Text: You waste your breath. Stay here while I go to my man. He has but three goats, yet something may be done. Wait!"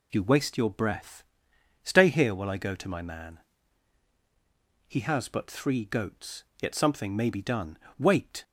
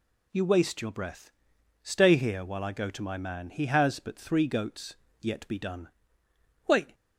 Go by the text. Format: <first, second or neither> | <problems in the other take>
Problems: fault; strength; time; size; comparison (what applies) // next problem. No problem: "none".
first | skips "something may"; at 5.4 s